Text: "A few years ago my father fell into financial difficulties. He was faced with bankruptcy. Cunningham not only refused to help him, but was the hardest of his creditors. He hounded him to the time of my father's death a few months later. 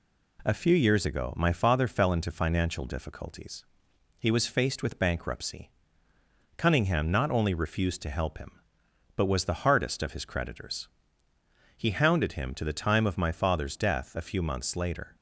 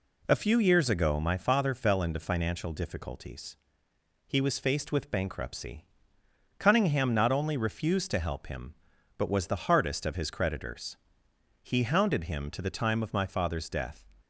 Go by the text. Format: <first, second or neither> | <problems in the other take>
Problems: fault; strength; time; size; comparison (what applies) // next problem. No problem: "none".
first | stops before "a few months later"; at 14.2 s